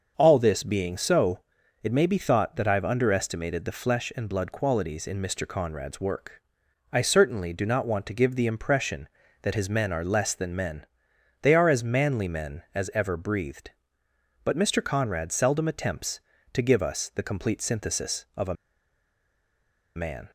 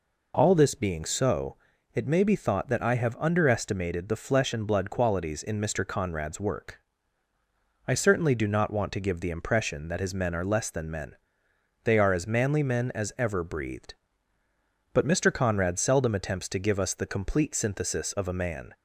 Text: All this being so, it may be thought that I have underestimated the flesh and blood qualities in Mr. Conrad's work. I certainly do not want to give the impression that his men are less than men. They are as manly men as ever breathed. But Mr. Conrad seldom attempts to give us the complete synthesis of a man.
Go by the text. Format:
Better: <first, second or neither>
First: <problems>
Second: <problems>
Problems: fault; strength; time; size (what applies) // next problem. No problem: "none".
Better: second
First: starts louder than the rest; until 1.1 s; 6.5 dB // pauses between "a" and "man"; strong; at 18.5 s; 1.4 s long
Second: none